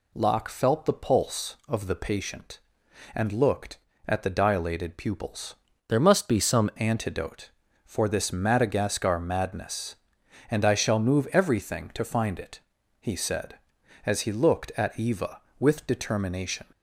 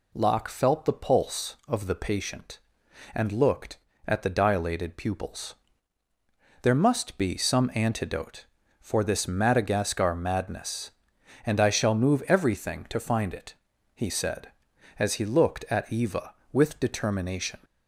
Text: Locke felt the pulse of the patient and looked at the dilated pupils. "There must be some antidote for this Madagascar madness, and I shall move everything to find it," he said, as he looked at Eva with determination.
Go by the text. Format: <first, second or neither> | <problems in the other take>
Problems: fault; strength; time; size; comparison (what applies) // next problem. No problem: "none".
second | changes voice from "There" to "some"; from 5.8 to 6.7 s; 0.9 s long